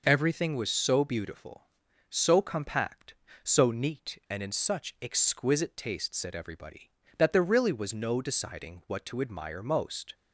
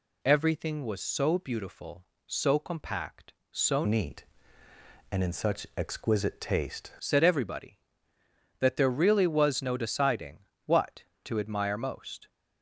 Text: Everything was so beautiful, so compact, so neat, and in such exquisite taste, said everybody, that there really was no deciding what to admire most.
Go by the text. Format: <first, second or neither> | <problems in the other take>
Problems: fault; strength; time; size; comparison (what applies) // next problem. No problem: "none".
first | changes voice from "neat" to "taste"; from 3.8 to 6.9 s; 3.1 s long // pauses between "deciding" and "what"; slight; at 10.3 s; 0.28 s long